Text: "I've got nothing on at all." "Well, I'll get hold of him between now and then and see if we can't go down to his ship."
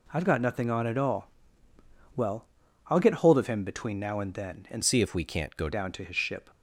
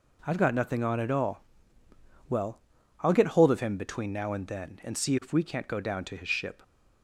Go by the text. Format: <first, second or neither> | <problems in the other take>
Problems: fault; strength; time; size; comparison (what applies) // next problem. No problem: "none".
second | changes voice from "see" to "go"; from 4.8 to 5.6 s; 0.8 s long